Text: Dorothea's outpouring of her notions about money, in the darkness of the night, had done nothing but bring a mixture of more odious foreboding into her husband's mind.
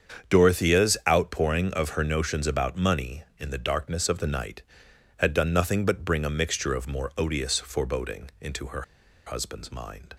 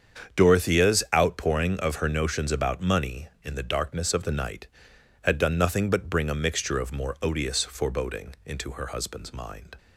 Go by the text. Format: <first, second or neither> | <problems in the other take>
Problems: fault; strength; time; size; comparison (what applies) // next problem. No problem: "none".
second | starts louder than the rest; strong; until 1.3 s; 7 dB; strong in the second // pauses between "her" and "husband's"; at 8.8 s; 0.44 s long